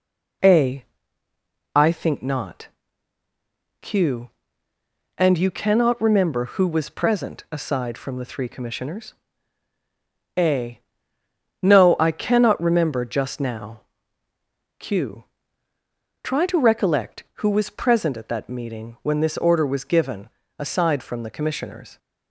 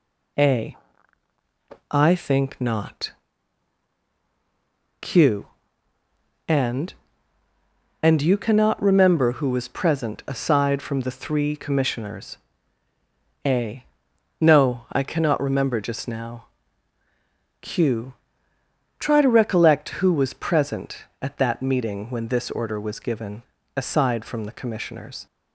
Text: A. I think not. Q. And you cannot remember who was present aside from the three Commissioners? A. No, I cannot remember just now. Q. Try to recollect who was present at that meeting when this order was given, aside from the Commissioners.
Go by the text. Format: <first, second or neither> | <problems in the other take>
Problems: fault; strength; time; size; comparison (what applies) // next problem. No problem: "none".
first | says "And" twice; at 8.0 s